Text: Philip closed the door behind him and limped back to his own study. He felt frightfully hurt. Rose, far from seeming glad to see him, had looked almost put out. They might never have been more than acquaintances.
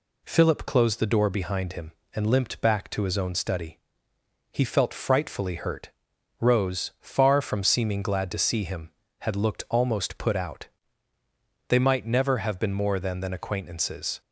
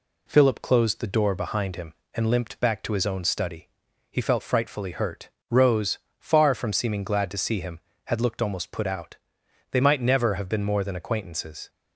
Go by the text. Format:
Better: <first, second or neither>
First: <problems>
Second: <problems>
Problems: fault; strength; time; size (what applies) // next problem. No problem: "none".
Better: second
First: says "than" twice; at 13.2 s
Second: none